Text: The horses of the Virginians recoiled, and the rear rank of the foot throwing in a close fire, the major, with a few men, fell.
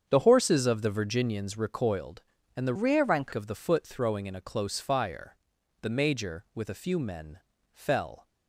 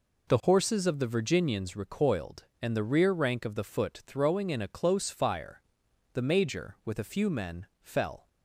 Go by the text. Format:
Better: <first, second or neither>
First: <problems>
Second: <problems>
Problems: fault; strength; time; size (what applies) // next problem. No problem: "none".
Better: second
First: starts louder than the rest; strong; until 1.1 s; 7.5 dB // changes voice from "rear" to "rank"; from 2.7 to 3.3 s; 0.6 s long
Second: none